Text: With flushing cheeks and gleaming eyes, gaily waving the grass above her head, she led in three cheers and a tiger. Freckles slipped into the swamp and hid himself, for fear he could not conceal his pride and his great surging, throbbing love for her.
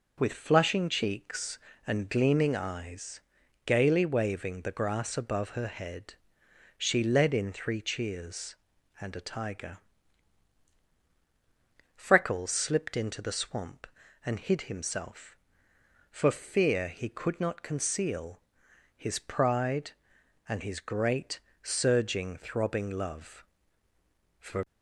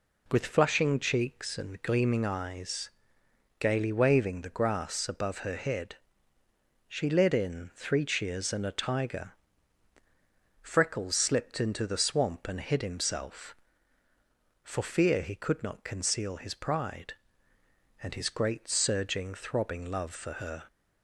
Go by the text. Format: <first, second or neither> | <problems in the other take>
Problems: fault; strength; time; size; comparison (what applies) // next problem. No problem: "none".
second | pauses between "conceal" and "his"; noticeable; at 18.4 s; 0.56 s long // pauses between "great" and "surging"; slight; at 21.3 s; 0.24 s long // stops before "her"; at 24.6 s